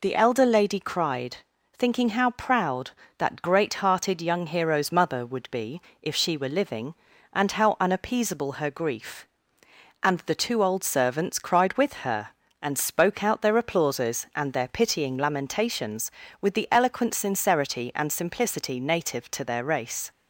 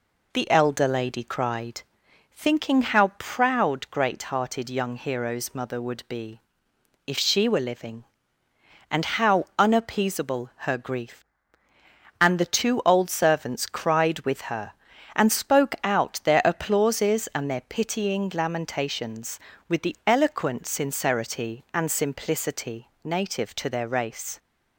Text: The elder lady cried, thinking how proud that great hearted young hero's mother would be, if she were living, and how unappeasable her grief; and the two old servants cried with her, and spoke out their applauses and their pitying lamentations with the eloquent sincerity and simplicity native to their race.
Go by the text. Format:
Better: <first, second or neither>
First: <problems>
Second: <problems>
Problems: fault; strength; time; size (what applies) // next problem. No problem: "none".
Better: first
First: none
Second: skips "that"; at 3.8 s // pauses between "simplicity" and "native"; slight; at 22.8 s; 0.16 s long